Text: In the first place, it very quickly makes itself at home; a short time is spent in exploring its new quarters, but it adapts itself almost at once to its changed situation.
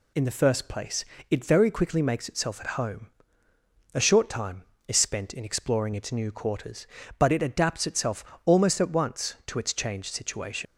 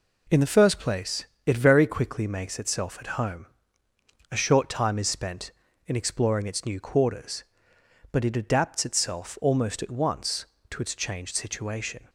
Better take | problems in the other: second | pauses between "itself" and "almost"; slight; at 8.2 s; 0.20 s long // leaves "situation" unfinished; at 10.6 s; 80 ms

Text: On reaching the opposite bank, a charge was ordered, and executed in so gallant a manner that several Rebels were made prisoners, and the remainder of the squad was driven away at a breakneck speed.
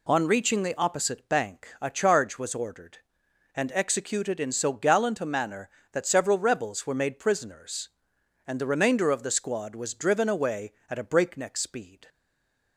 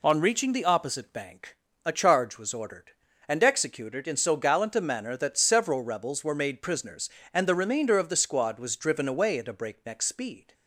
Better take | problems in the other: second | stays silent after the last word; slight; from 12.0 s on; 0.7 s long

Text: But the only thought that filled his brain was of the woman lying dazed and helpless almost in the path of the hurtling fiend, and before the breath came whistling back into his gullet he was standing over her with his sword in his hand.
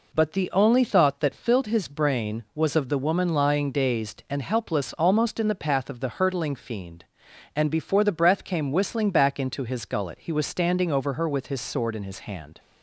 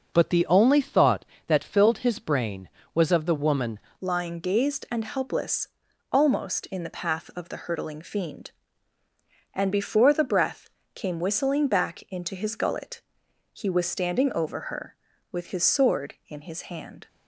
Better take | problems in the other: first | changes voice at "lying"; from 4.0 s on; 13.0 s long // pauses between "helpless" and "almost"; at 5.6 s; 0.42 s long // pauses between "breath" and "came"; slight; at 10.6 s; 0.24 s long // pauses between "gullet" and "he"; noticeable; at 13.0 s; 0.52 s long

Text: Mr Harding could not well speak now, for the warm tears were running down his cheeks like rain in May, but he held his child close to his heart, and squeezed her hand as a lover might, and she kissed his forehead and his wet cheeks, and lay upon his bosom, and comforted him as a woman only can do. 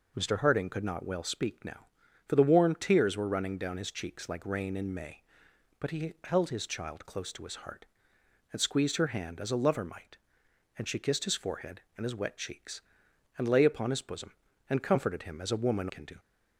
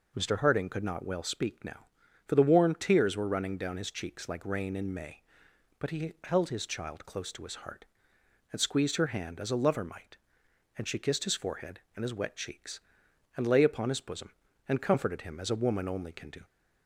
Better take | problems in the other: second | skips "only"; at 15.8 s

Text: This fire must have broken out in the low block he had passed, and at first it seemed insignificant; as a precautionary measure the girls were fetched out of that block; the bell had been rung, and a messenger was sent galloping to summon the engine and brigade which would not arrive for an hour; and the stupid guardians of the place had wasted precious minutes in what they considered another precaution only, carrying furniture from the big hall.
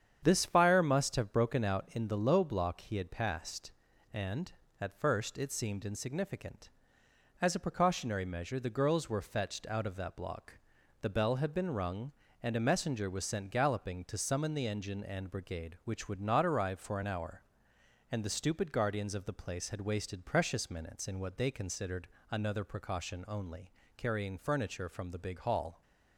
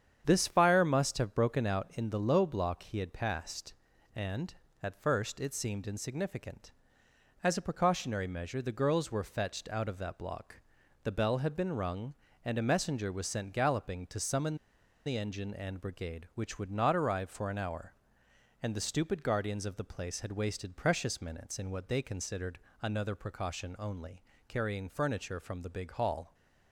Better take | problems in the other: first | starts louder than the rest; strong; until 1.2 s; 8.5 dB; strong in the first // pauses between "summon" and "the"; noticeable; at 14.5 s; 0.50 s long // pauses between "considered" and "another"; slight; at 22.5 s; 0.24 s long; slight in the first

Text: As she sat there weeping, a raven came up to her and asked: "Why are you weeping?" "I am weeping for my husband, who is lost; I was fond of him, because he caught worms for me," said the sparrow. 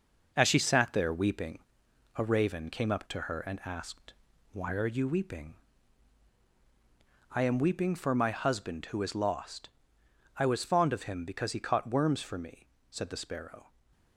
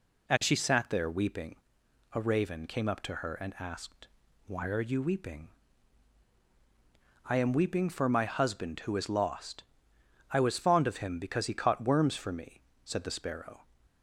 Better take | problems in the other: second | gets quieter; noticeable; throughout; 5 dB

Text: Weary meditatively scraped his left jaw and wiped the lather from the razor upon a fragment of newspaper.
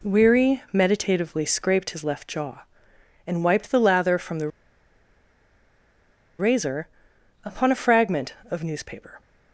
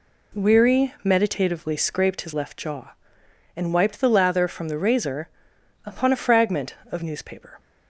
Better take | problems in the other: second | pauses between "the" and "razor"; strong; at 4.4 s; 1.9 s long // pauses between "razor" and "upon"; noticeable; at 6.8 s; 0.58 s long; noticeable in the second

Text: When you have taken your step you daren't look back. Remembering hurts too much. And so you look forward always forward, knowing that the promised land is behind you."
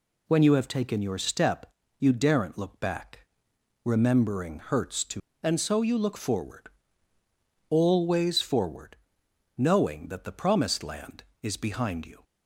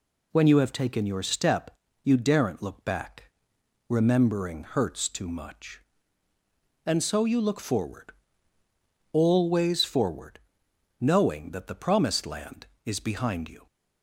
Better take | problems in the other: second | pauses between "step" and "you"; slight; at 1.6 s; 0.32 s long; slight in the second // skips "much"; at 5.3 s // pauses between "forward" and "always"; at 6.6 s; 1.0 s long; also in the second

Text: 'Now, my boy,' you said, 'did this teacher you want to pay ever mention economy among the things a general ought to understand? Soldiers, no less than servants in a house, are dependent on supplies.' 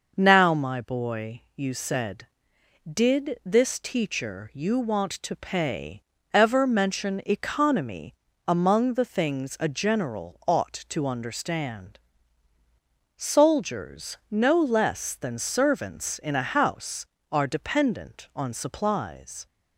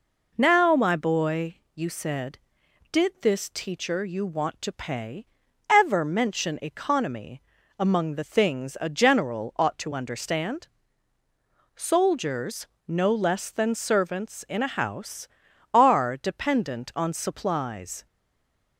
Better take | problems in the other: first | pauses between "pay" and "ever"; at 5.2 s; 0.42 s long; slight in the first // pauses between "economy" and "among"; slight; at 7.4 s; 0.36 s long; slight in the first // stays silent after the last word; slight; from 18.0 s on; 0.7 s long

